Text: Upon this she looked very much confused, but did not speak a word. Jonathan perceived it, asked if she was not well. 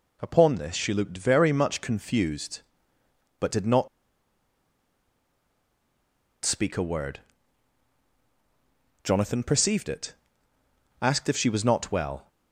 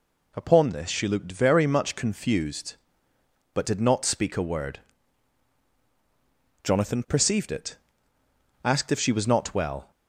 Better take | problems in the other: second | pauses between "not" and "speak"; strong; at 3.8 s; 2.5 s long

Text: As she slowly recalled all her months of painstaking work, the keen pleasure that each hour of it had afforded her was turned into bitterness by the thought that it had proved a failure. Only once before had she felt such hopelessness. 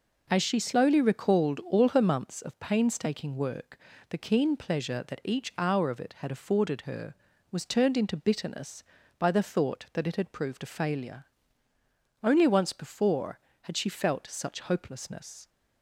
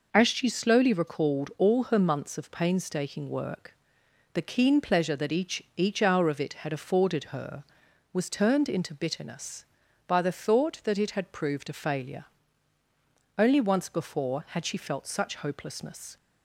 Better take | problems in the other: first | says "each" twice; at 5.7 s

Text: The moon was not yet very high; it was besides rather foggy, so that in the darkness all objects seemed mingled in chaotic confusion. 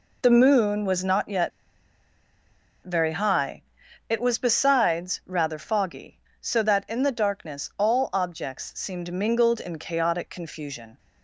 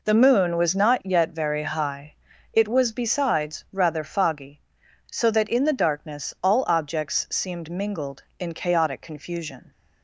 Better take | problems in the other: second | pauses between "yet" and "very"; strong; at 1.5 s; 1.3 s long

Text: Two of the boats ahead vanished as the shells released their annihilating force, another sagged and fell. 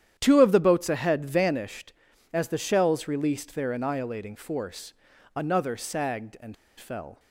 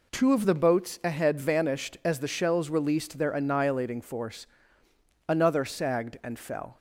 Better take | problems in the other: second | starts louder than the rest; strong; until 1.1 s; 10 dB // pauses between "and" and "fell"; slight; at 6.5 s; 0.24 s long

